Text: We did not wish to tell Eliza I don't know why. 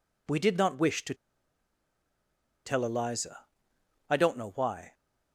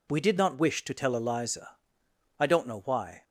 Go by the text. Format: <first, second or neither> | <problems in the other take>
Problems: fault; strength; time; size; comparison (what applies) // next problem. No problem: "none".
second | pauses between "to" and "tell"; strong; at 1.1 s; 1.5 s long // pauses between "Eliza" and "I"; noticeable; at 3.4 s; 0.64 s long; noticeable in the second